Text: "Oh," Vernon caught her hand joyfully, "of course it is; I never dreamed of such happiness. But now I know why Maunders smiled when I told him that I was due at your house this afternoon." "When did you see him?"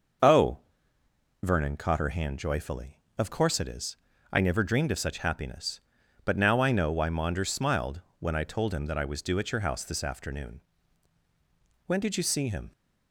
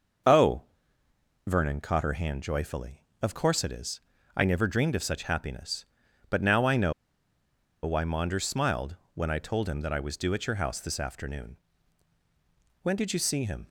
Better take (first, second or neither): first